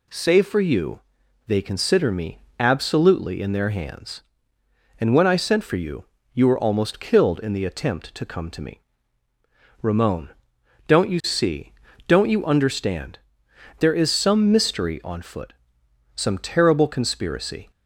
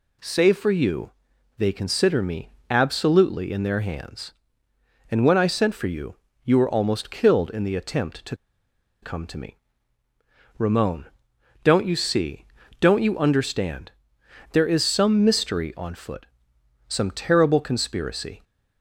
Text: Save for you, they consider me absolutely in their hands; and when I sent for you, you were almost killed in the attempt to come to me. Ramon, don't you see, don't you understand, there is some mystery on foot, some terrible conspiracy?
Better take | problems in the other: first | pauses between "me" and "absolutely"; slight; at 2.5 s; 0.18 s long; slight in the first // pauses between "to" and "come"; noticeable; at 8.3 s; 0.66 s long

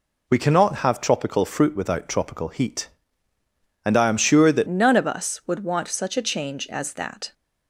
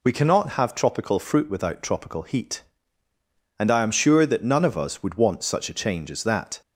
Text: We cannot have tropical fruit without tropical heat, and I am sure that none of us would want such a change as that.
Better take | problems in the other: second | changes voice at "none"; from 4.6 s on; 2.7 s long

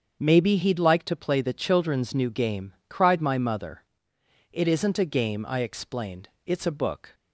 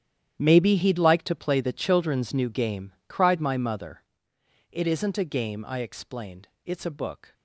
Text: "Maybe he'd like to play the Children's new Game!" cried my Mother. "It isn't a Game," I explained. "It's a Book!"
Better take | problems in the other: first | gets quieter; strong; throughout; 15.5 dB // starts louder than the rest; strong; until 1.4 s; 10.5 dB; also in the first

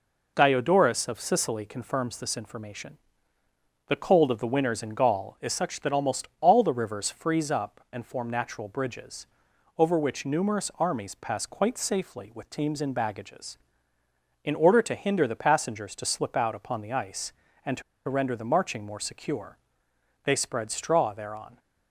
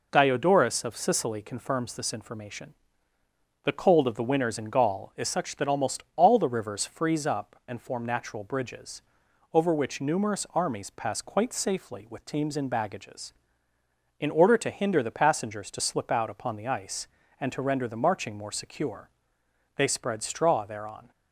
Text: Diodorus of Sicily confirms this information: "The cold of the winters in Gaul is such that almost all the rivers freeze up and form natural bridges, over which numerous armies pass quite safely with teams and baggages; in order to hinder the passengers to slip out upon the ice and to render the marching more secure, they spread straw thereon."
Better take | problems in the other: second | pauses between "to" and "render"; slight; at 17.8 s; 0.25 s long

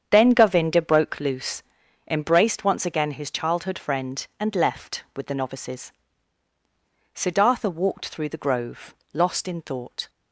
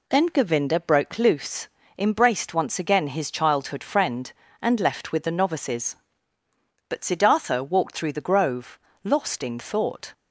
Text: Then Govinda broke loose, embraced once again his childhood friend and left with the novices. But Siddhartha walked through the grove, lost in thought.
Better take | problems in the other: second | starts louder than the rest; strong; until 1.1 s; 8 dB // skips "But"; at 6.5 s

